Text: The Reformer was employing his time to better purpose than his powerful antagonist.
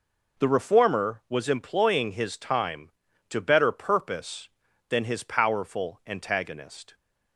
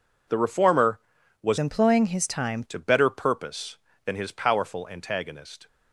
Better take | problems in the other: first | changes voice from "employing" to "time"; from 1.5 to 2.6 s; 1.1 s long

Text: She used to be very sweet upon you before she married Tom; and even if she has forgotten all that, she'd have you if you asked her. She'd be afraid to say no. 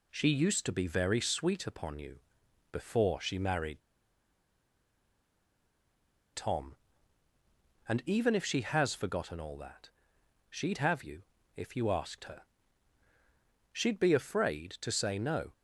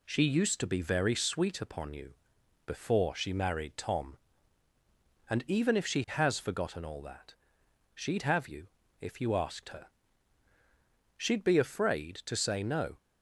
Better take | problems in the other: second | pauses between "you" and "before"; noticeable; at 2.1 s; 0.52 s long; noticeable in the second // pauses between "married" and "Tom"; strong; at 3.8 s; 2.5 s long // pauses between "you" and "if"; slight; at 11.2 s; 0.34 s long; slight in the second

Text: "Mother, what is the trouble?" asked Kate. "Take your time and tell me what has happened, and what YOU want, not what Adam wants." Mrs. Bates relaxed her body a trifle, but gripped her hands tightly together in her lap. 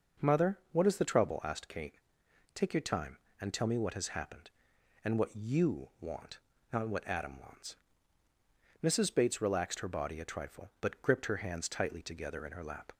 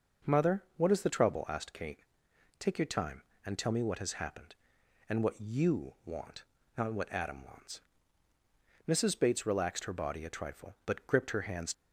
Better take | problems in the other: first | stops before "tightly together in her lap"; at 11.7 s

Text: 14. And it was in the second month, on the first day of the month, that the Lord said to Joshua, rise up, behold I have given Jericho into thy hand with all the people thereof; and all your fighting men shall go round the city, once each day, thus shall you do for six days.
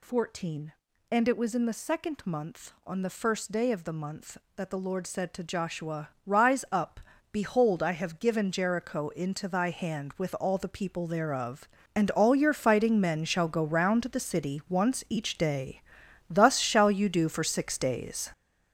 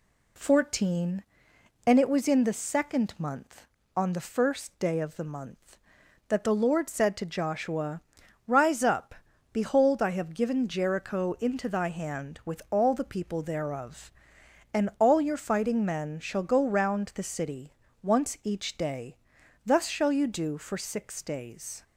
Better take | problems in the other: second | gets louder; strong; throughout; 8 dB

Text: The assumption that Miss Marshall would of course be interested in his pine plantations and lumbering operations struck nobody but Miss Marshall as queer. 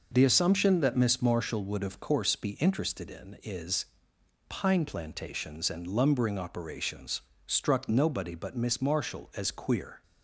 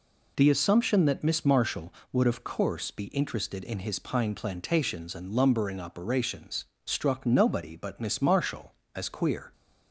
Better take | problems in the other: second | says "is" for "his"; at 3.4 s // pauses between "operations" and "struck"; slight; at 7.2 s; 0.24 s long; slight in the second

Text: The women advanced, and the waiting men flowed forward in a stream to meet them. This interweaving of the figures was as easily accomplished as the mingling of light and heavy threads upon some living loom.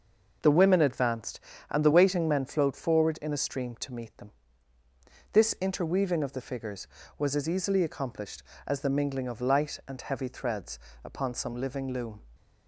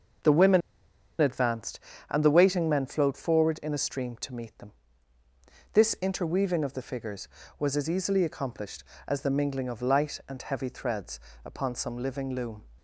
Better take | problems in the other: first | pauses between "women" and "advanced"; noticeable; at 0.6 s; 0.59 s long // pauses between "threads" and "upon"; slight; at 11.1 s; 0.24 s long; slight in the first

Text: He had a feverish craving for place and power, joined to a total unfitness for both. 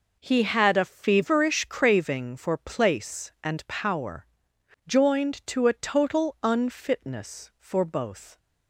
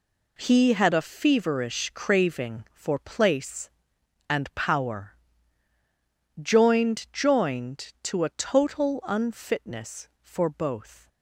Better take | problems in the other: first | says "joined" twice; at 7.1 s

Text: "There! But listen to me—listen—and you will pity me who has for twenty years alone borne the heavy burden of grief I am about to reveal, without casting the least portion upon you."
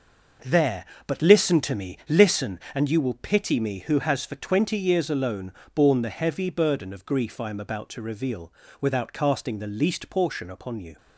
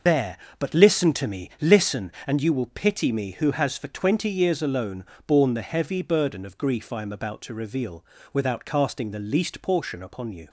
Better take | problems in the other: first | loses the start of "There"; at 0.0 s; 120 ms // pauses between "alone" and "borne"; slight; at 5.0 s; 0.22 s long; slight in the first

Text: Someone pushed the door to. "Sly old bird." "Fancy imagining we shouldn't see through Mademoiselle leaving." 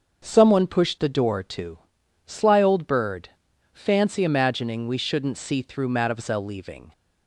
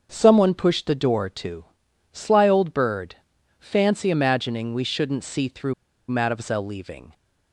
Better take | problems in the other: first | starts louder than the rest; until 1.1 s; 6.5 dB; also in the first // pauses between "through" and "Mademoiselle"; at 5.7 s; 0.37 s long

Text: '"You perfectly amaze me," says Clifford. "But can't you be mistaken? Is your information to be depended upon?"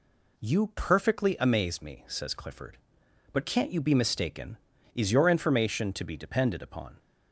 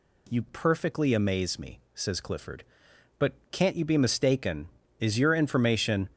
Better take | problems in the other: first | pauses between "But" and "can't"; slight; at 3.3 s; 0.18 s long // stops before "to be depended upon"; at 6.1 s

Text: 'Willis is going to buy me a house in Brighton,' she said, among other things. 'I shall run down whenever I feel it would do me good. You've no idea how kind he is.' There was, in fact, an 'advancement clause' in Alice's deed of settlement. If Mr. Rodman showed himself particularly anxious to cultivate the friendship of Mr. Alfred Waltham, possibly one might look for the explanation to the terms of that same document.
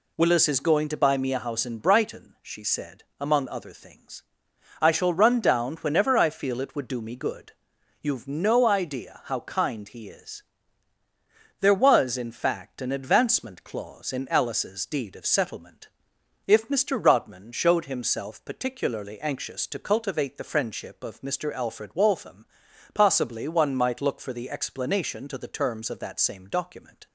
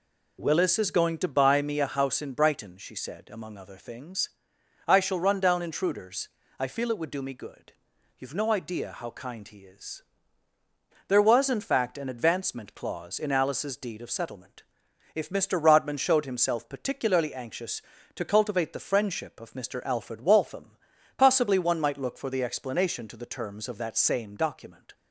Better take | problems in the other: first | says "intruders" for "whenever"; at 5.6 s

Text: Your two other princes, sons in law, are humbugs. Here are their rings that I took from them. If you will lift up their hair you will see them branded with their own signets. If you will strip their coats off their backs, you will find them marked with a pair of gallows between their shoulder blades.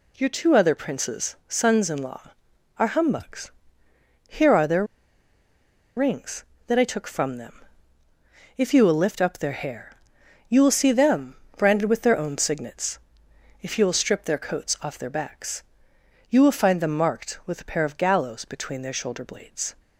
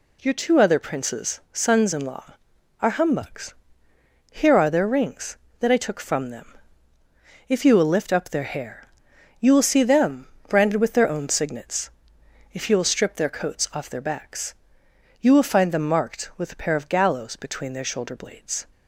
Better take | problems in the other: second | pauses between "their" and "rings"; at 4.8 s; 1.1 s long // pauses between "hair" and "you"; noticeable; at 9.9 s; 0.54 s long; noticeable in the second // pauses between "them" and "branded"; slight; at 11.3 s; 0.22 s long; slight in the second

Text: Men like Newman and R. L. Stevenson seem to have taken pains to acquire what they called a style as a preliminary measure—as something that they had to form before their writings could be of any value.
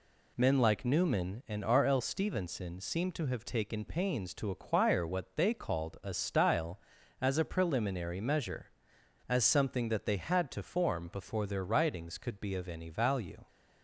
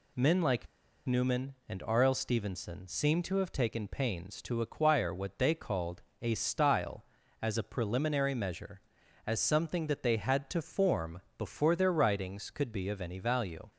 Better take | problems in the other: first | pauses between "like" and "Newman"; at 0.6 s; 0.39 s long // pauses between "called" and "a"; slight; at 6.0 s; 0.18 s long // pauses between "form" and "before"; slight; at 11.2 s; 0.16 s long

